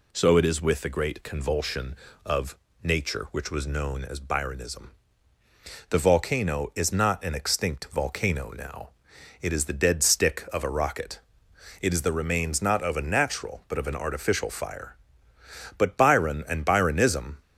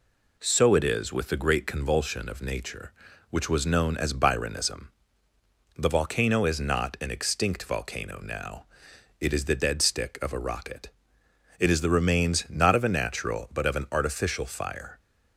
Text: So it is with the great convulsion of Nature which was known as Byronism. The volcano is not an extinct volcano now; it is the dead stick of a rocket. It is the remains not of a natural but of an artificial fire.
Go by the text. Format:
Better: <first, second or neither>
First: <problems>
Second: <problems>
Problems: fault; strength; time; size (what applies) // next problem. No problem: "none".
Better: second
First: pauses between "of" and "Nature"; slight; at 2.5 s; 0.26 s long // goes on to say "But Byron and Byronism"; from 15.7 s on; 1.6 s long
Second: none